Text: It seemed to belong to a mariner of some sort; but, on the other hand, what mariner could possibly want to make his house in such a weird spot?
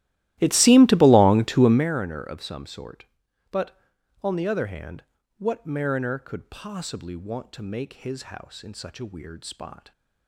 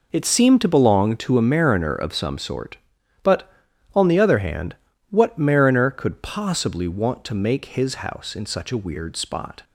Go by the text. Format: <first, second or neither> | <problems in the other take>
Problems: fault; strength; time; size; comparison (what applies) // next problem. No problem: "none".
second | starts louder than the rest; strong; until 1.9 s; 15.5 dB